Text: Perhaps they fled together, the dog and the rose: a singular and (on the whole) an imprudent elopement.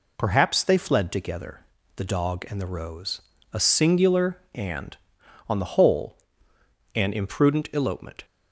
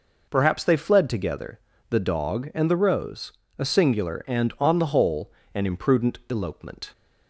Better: neither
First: none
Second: none

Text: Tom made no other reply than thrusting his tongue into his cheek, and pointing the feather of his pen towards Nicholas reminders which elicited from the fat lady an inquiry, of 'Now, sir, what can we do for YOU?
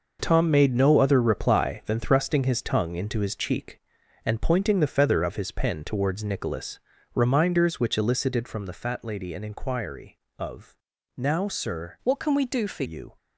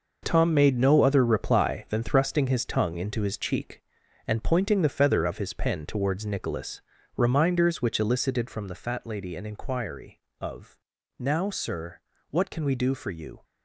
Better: second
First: pauses between "Nicholas" and "reminders"; slight; at 6.7 s; 0.34 s long // pauses between "of" and "Now"; at 10.7 s; 0.40 s long // changes voice from "what" to "for"; from 12.0 to 12.8 s; 0.8 s long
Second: pauses between "Nicholas" and "reminders"; slight; at 6.8 s; 0.34 s long // pauses between "of" and "Now"; at 10.7 s; 0.40 s long

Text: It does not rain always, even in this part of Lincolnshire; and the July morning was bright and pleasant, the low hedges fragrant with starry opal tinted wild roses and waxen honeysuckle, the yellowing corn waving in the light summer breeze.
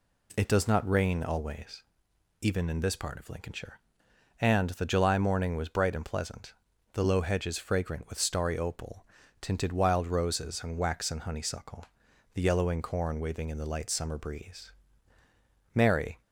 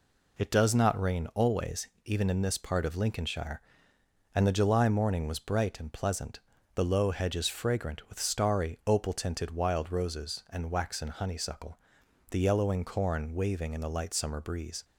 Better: second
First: pauses between "opal" and "tinted"; slight; at 9.0 s; 0.36 s long // goes on to say "Mary"; slight; from 15.7 s on; 0.46 s long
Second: none

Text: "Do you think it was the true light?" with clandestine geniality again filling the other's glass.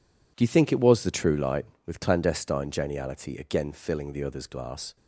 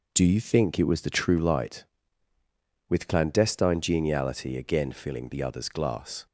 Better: neither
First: none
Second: none

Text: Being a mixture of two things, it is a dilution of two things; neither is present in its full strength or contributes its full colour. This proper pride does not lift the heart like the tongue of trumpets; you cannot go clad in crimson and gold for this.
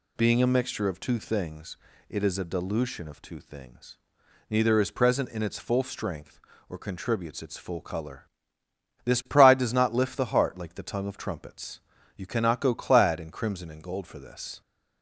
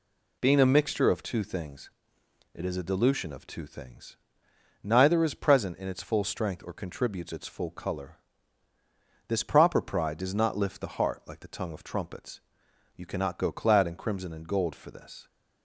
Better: second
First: skips "proper"; at 9.2 s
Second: none

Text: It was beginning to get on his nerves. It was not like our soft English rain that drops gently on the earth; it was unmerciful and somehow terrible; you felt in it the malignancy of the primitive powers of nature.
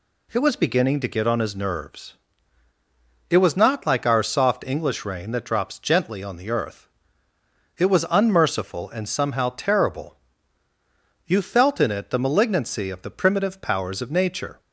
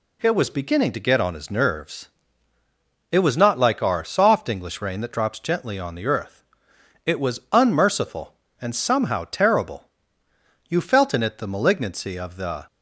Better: first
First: none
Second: stops before "primitive powers of nature"; at 12.6 s

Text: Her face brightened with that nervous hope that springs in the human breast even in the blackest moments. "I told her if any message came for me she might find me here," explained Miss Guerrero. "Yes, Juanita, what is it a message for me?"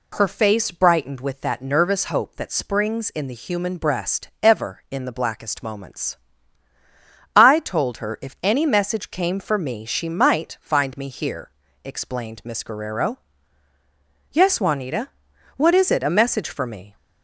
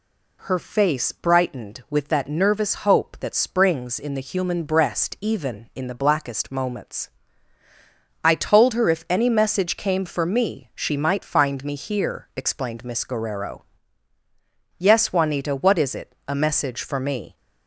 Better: second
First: says "ever" for "even"; at 4.4 s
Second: none

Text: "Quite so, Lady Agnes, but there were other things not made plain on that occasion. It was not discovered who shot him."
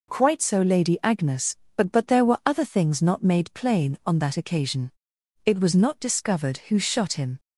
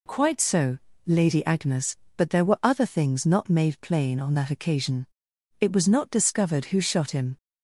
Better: second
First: says "but" twice; at 1.9 s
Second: none

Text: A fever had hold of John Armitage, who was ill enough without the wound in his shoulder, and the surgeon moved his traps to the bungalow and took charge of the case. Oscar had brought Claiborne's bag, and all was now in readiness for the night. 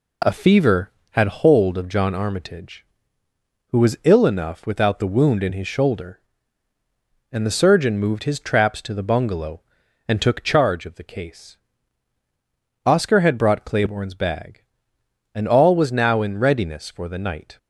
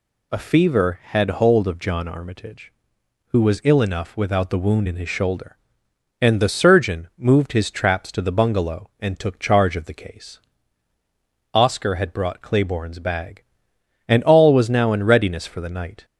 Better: neither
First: none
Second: none

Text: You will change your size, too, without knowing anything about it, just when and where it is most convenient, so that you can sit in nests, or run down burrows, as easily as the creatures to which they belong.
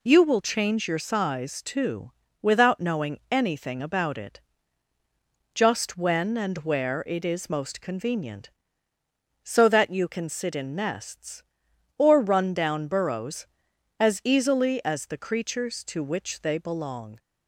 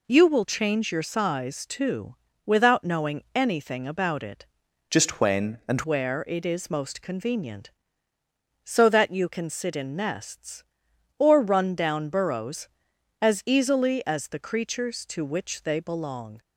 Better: first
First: none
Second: changes voice from "just" to "and"; from 4.8 to 5.7 s; 0.9 s long

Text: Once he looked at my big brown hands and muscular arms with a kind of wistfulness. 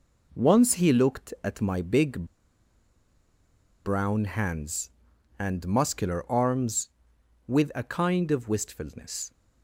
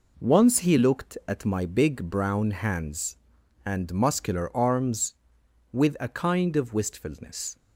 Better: second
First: pauses between "big" and "brown"; strong; at 2.2 s; 1.6 s long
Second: none

